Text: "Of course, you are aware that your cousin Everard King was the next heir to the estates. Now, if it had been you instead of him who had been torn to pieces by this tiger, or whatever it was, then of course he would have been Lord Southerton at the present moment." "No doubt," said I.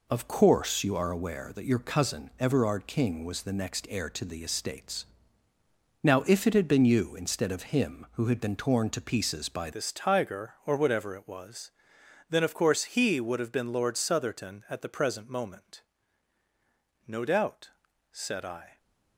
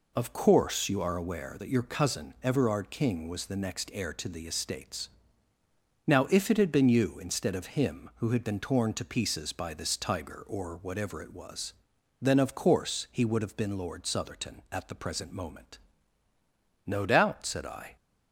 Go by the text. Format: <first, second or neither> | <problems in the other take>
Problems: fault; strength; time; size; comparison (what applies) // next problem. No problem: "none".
second | changes voice at "this"; from 9.7 s on; 9.0 s long